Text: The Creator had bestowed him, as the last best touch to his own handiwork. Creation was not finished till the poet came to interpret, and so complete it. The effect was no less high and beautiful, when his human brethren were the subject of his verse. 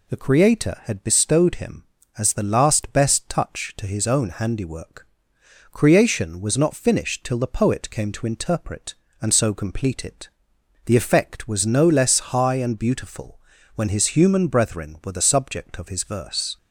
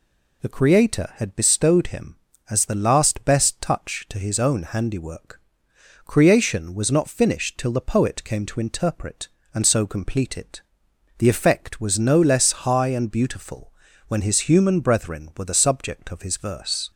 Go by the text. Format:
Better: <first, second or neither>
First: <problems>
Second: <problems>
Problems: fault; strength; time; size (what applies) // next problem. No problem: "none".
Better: neither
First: none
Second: none